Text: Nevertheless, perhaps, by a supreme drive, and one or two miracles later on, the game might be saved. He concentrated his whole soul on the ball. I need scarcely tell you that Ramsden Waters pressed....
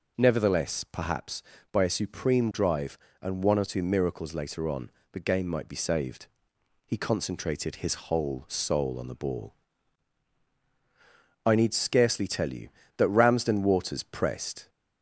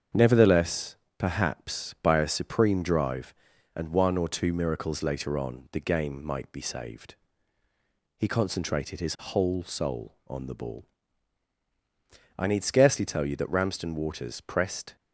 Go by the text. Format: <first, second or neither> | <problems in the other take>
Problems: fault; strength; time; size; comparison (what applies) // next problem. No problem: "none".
first | gets quieter; noticeable; throughout; 5 dB